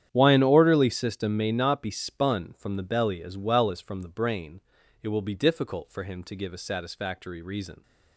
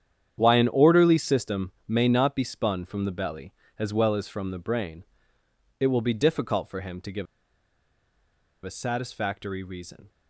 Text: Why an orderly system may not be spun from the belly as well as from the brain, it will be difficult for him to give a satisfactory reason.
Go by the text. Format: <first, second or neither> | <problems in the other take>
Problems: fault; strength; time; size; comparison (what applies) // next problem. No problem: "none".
first | starts louder than the rest; strong; until 1.3 s; 9 dB; strong in the first // pauses between "give" and "a"; strong; at 7.2 s; 1.3 s long